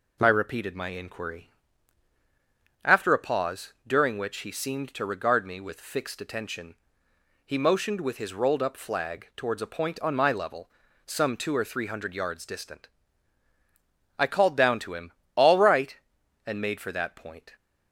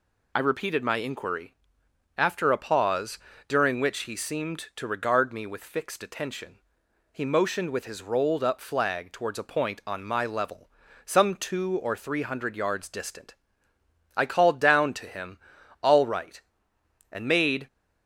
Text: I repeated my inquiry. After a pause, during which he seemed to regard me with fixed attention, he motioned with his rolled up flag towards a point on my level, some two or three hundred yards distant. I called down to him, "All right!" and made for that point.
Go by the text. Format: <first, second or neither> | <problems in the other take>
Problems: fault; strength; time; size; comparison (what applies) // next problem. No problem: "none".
first | stops before "for that point"; at 17.6 s